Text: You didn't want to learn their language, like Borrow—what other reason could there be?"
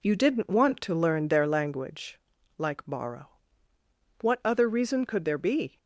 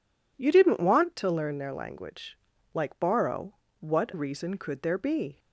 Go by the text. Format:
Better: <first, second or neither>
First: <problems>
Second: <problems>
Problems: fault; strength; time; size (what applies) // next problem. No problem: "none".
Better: first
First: none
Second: skips "other"; at 4.1 s